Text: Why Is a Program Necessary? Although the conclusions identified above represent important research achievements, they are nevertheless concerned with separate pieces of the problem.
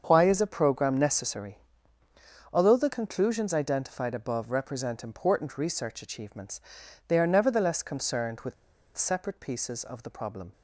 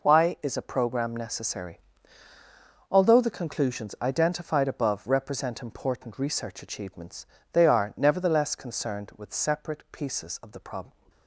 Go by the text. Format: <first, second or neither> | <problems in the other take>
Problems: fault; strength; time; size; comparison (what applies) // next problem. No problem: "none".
second | starts louder than the rest; until 1.0 s; 7 dB // pauses between "with" and "separate"; at 8.5 s; 0.41 s long